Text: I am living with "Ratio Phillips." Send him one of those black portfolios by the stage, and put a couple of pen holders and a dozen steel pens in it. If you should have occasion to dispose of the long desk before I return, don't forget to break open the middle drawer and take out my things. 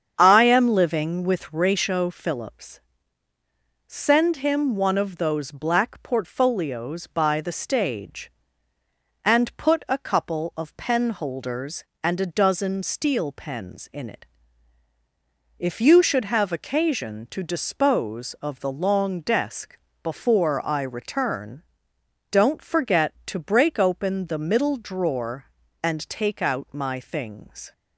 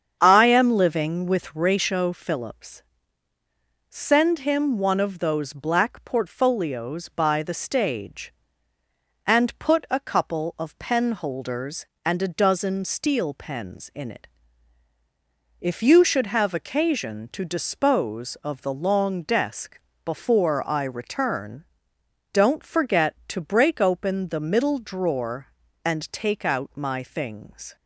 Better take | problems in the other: neither | starts louder than the rest; strong; the same in both // pauses between "desk" and "before"; slight; the same in both

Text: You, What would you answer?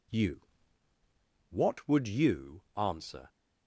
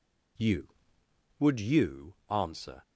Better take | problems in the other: first | skips "What"; at 1.0 s

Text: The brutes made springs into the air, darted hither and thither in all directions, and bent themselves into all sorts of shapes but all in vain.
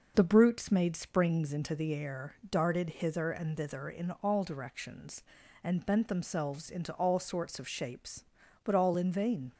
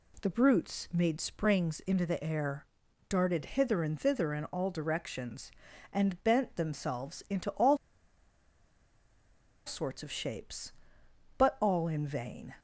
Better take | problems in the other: first | pauses between "all" and "sorts"; strong; at 7.7 s; 1.8 s long

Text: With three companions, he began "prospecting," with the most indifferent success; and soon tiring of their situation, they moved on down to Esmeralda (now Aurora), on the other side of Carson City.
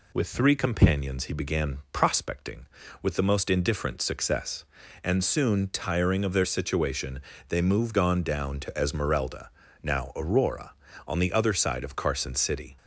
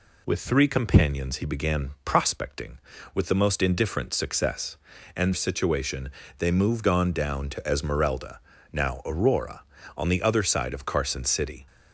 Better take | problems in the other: first | skips "soon tiring of their"; at 5.3 s

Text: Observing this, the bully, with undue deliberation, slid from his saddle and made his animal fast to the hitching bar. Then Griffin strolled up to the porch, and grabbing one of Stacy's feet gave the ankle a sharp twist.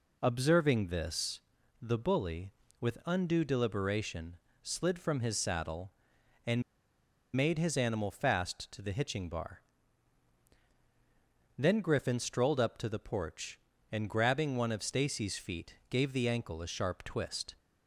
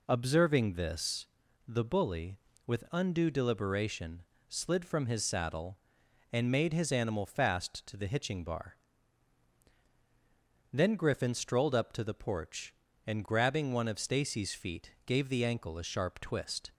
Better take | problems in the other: second | pauses between "and" and "made"; noticeable; at 6.6 s; 0.74 s long // pauses between "feet" and "gave"; slight; at 15.7 s; 0.16 s long; slight in the second

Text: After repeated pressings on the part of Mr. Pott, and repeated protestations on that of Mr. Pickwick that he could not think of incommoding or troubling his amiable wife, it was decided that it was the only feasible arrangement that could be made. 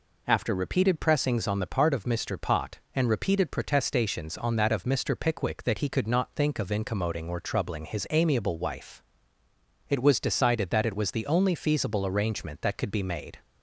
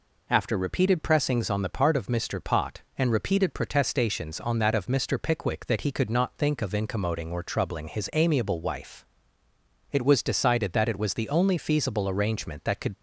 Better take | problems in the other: first | stops before "be made"; at 12.9 s

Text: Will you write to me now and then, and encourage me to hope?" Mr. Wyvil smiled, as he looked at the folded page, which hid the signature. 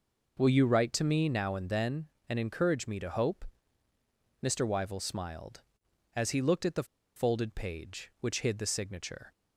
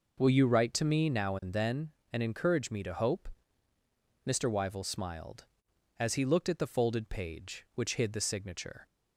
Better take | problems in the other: second | pauses between "the" and "folded"; slight; at 6.8 s; 0.32 s long

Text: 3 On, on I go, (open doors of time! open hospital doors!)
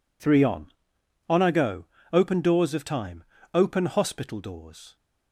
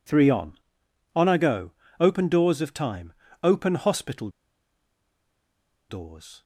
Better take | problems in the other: first | pauses between "hospital" and "doors"; strong; at 4.2 s; 1.6 s long

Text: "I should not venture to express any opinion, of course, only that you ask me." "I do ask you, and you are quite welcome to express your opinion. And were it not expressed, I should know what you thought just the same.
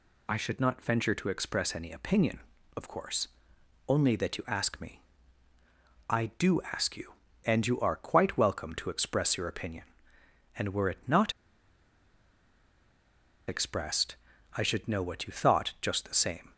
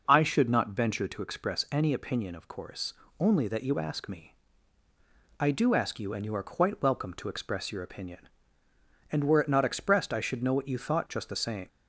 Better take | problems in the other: second | pauses between "not" and "expressed"; strong; at 11.3 s; 2.1 s long

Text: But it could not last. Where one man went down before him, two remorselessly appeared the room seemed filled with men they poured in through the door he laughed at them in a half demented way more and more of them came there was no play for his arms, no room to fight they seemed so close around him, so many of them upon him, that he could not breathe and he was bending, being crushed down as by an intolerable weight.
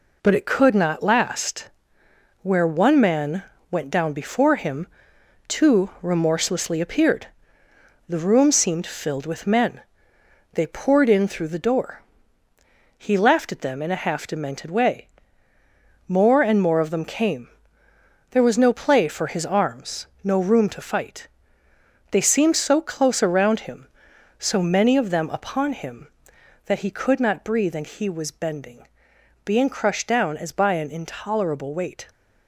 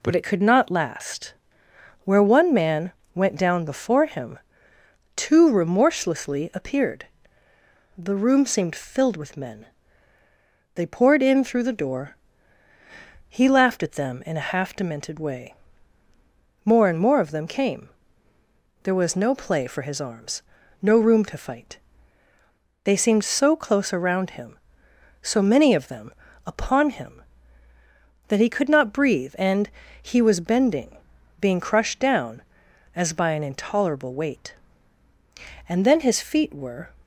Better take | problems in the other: first | pauses between "man" and "went"; slight; at 2.9 s; 0.22 s long; slight in the first // pauses between "appeared" and "the"; noticeable; at 7.0 s; 0.92 s long; noticeable in the first // pauses between "men" and "they"; at 9.6 s; 1.1 s long; noticeable in the first // pauses between "door" and "he"; at 12.1 s; 1.1 s long; noticeable in the first // pauses between "way" and "more"; at 15.5 s; 1.1 s long; also in the first // pauses between "came" and "there"; noticeable; at 17.8 s; 0.94 s long; noticeable in the first // pauses between "fight" and "they"; at 21.7 s; 1.0 s long; noticeable in the first // pauses between "them" and "upon"; slight; at 26.0 s; 0.36 s long // pauses between "and" and "he"; slight; at 29.6 s; 0.34 s long // goes on to say "And then his feet were"; noticeable; from 35.6 s on; 1.2 s long

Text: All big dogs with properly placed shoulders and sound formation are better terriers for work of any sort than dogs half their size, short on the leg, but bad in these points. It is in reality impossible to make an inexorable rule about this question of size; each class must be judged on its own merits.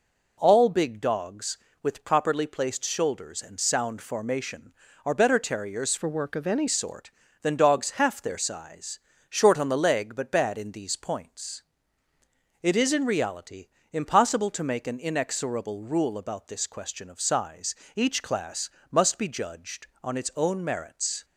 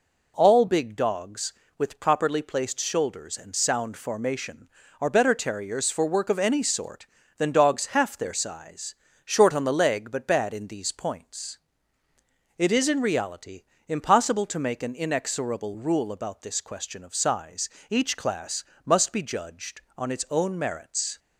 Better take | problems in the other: second | changes voice from "for" to "any"; from 5.9 to 6.6 s; 0.7 s long // pauses between "reality" and "impossible"; slight; at 13.6 s; 0.24 s long; slight in the second // pauses between "class" and "must"; slight; at 18.7 s; 0.22 s long; slight in the second

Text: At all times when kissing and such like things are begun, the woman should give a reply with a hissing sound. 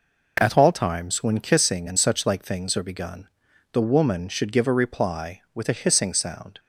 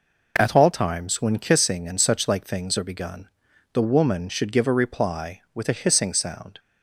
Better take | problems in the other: neither | none

